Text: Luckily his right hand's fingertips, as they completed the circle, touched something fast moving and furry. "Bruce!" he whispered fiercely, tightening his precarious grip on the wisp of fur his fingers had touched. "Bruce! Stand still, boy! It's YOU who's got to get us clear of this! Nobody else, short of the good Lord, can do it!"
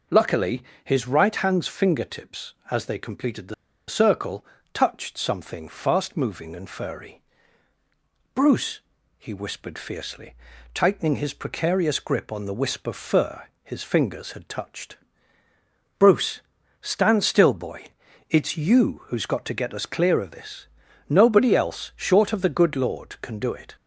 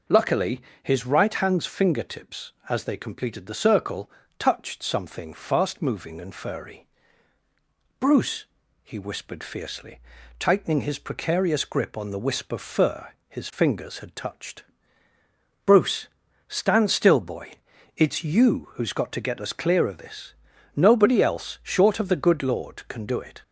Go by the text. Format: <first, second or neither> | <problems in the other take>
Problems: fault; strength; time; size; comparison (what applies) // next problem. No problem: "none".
second | pauses between "Luckily" and "his"; slight; at 0.6 s; 0.22 s long; slight in the second // pauses between "the" and "circle"; slight; at 3.5 s; 0.35 s long // pauses between "fur" and "his"; slight; at 13.4 s; 0.16 s long; slight in the second